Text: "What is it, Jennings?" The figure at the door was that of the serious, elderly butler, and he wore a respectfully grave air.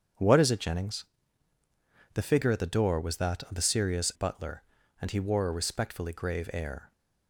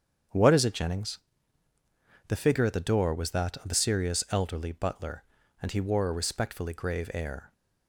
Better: second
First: starts louder than the rest; strong; until 2.2 s; 7.5 dB // skips "elderly"; at 4.1 s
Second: starts louder than the rest; strong; until 2.3 s; 7.5 dB

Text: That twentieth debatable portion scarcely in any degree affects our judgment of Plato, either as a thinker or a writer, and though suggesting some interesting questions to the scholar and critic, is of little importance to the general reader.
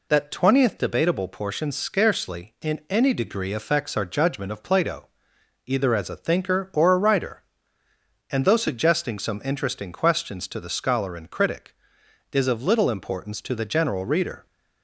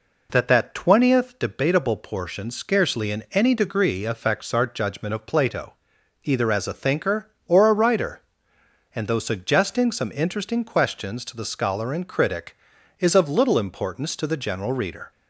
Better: first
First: none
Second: says "That" twice; at 0.4 s

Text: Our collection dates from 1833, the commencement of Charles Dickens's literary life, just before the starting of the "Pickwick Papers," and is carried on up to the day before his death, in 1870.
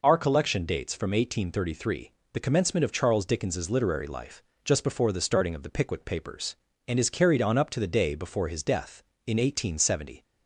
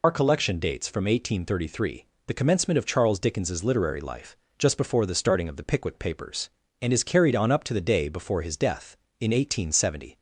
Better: first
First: none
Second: loses the start of "Our"; at 0.0 s; 75 ms

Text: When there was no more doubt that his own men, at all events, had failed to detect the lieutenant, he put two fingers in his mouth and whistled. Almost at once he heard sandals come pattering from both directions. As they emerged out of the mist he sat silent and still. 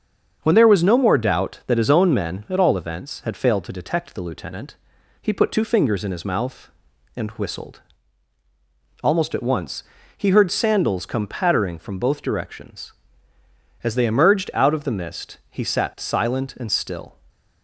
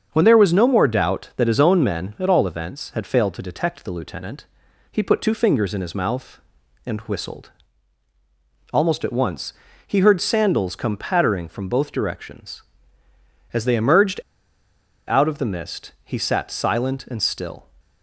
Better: first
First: starts louder than the rest; until 1.4 s; 7 dB // pauses between "once" and "he"; slight; at 9.8 s; 0.32 s long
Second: starts louder than the rest; until 1.1 s; 7 dB // pauses between "once" and "he"; slight; at 9.5 s; 0.32 s long // pauses between "emerged" and "out"; noticeable; at 14.1 s; 0.88 s long

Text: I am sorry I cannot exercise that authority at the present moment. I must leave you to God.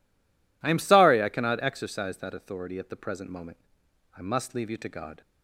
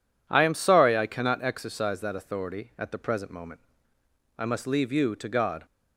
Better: second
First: stays silent before the first word; slight; until 0.6 s; 0.6 s long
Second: none

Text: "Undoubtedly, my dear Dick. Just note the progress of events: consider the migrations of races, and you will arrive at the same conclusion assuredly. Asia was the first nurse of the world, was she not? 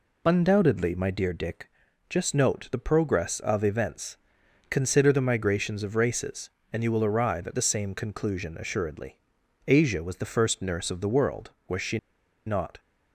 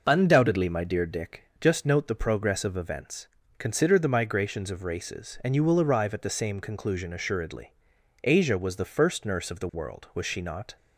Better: second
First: pauses between "she" and "not"; noticeable; at 11.9 s; 0.50 s long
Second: none

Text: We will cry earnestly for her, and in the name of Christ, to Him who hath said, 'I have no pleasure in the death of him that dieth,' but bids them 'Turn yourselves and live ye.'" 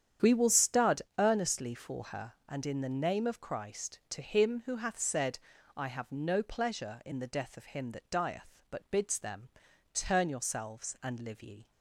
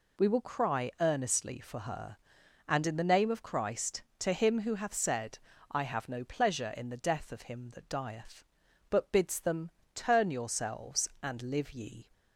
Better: second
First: starts louder than the rest; strong; until 1.3 s; 9 dB // says "stud" for "cry"; at 0.5 s // pauses between "them" and "Turn"; noticeable; at 9.4 s; 0.46 s long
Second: pauses between "them" and "Turn"; slight; at 9.7 s; 0.24 s long

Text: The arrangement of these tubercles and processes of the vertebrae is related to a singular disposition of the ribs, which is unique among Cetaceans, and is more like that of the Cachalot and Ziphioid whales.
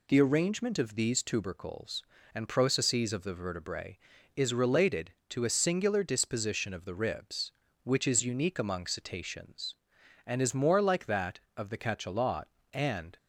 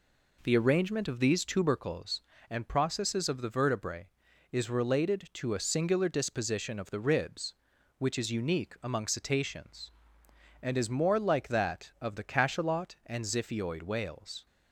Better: second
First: stops before "Ziphioid whales"; at 13.1 s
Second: none

